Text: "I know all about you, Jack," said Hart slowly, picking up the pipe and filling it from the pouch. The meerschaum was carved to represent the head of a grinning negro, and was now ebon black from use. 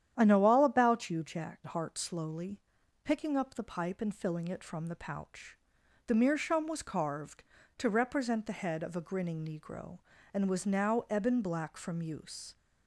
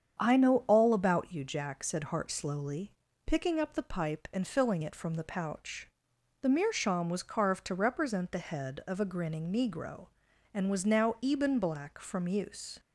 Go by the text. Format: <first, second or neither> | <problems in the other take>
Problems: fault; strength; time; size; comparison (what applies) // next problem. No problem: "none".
second | starts louder than the rest; strong; until 1.1 s; 10 dB; strong in the second // skips "said"; at 1.6 s